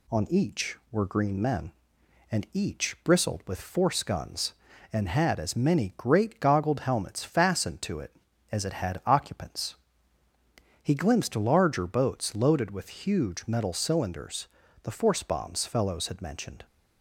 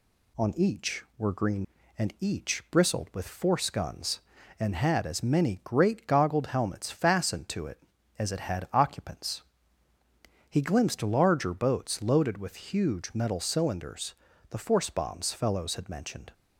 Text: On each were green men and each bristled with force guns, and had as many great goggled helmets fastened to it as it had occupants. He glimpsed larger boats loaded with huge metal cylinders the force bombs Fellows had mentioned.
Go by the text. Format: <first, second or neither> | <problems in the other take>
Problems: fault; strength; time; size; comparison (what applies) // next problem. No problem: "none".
first | skips "men"; at 1.8 s // pauses between "cylinders" and "the"; slight; at 14.1 s; 0.36 s long; slight in the first